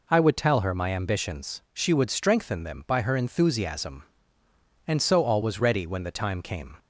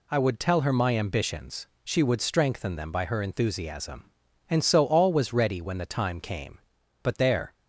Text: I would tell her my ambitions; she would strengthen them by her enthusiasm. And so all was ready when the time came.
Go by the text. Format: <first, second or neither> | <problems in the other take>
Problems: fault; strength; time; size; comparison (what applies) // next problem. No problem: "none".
first | goes on to say "But there"; from 7.0 s on; 0.52 s long